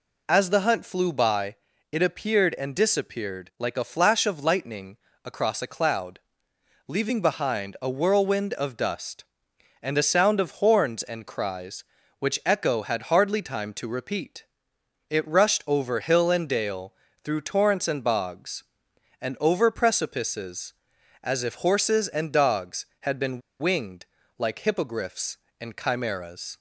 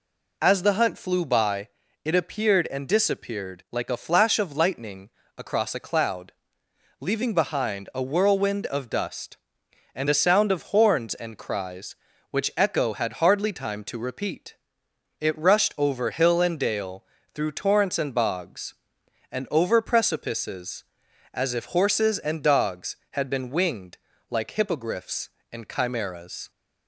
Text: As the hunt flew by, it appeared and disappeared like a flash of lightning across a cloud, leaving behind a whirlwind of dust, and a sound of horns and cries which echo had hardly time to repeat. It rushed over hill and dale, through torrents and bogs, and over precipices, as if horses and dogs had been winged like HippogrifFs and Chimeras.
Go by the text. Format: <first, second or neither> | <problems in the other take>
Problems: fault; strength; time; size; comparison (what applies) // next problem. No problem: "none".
second | pauses between "lightning" and "across"; slight; at 4.9 s; 0.26 s long; slight in the second // pauses between "been" and "winged"; slight; at 23.3 s; 0.20 s long // pauses between "winged" and "like"; slight; at 24.0 s; 0.32 s long; slight in the second